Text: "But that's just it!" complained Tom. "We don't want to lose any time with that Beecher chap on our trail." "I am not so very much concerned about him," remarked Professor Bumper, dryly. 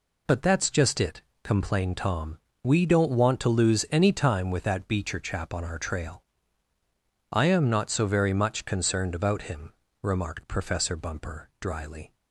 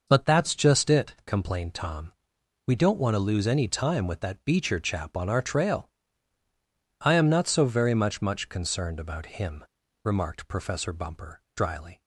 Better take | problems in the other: first | says "much" twice; at 8.2 s

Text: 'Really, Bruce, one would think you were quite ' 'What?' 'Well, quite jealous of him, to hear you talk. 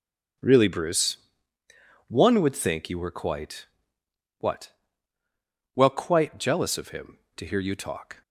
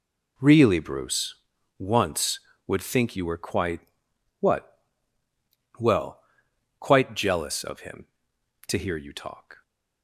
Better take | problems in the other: first | says "once" for "one"; at 1.7 s

